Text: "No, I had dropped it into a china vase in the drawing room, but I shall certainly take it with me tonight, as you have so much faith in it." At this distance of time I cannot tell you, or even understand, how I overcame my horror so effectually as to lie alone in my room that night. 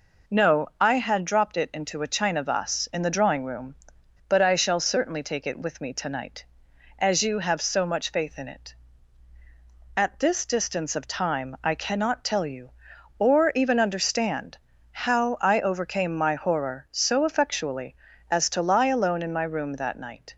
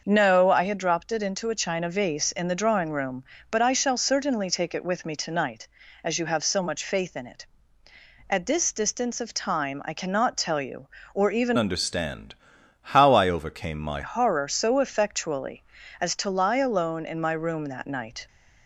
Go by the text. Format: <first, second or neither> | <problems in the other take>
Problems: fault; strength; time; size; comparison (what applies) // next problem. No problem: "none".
first | starts louder than the rest; noticeable; until 1.0 s; 6 dB // changes voice from "understand" to "my"; from 11.5 to 13.9 s; 2.4 s long